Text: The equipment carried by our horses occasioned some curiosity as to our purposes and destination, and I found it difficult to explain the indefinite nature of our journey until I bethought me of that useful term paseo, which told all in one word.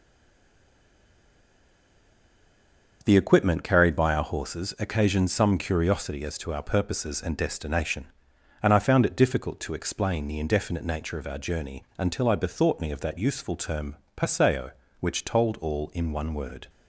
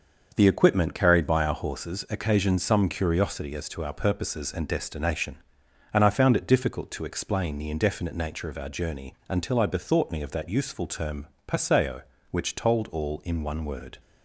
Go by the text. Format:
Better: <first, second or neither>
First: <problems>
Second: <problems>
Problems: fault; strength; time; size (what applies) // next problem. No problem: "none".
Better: second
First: stays silent before the first word; strong; until 3.0 s; 3.0 s long // starts louder than the rest; until 4.0 s; 6 dB // pauses between "journey" and "until"; slight; at 11.8 s; 0.16 s long // pauses between "term" and "paseo"; slight; at 13.9 s; 0.18 s long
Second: starts louder than the rest; until 1.3 s; 6 dB // pauses between "journey" and "until"; slight; at 9.1 s; 0.16 s long // pauses between "term" and "paseo"; slight; at 11.2 s; 0.18 s long